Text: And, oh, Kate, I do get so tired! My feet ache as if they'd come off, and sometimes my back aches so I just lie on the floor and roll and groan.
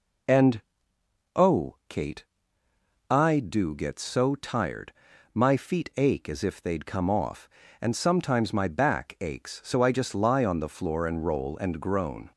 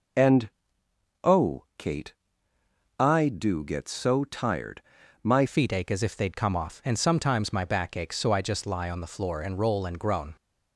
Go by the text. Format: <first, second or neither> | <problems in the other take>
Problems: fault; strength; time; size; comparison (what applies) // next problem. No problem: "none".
first | changes voice at "feet"; from 5.4 s on; 4.9 s long